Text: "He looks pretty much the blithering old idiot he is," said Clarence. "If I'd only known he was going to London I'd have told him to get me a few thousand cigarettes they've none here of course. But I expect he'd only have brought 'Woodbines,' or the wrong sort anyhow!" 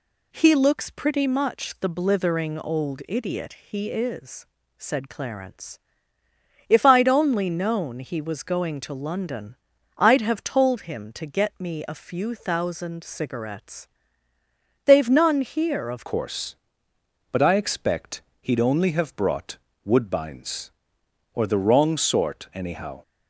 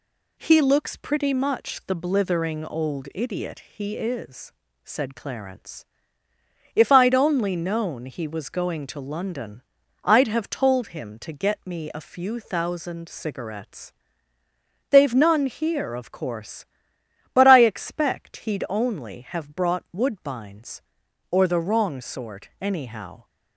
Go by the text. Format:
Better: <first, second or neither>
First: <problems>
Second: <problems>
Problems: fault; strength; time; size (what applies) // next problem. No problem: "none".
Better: second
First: pauses between "London" and "I'd"; at 9.5 s; 0.42 s long // pauses between "cigarettes" and "they've"; noticeable; at 13.8 s; 0.98 s long // changes voice at "course"; from 16.0 s on; 7.0 s long // pauses between "expect" and "he'd"; slight; at 18.2 s; 0.18 s long // pauses between "brought" and "Woodbines"; slight; at 19.5 s; 0.26 s long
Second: pauses between "London" and "I'd"; at 9.6 s; 0.42 s long // pauses between "cigarettes" and "they've"; noticeable; at 13.9 s; 0.98 s long